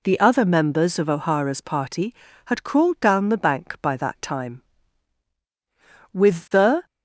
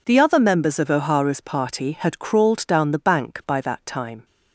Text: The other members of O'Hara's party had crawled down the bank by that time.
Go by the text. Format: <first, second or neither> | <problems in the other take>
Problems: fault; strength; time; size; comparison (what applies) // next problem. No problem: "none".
second | goes on to say "With the"; noticeable; from 6.1 s on; 0.73 s long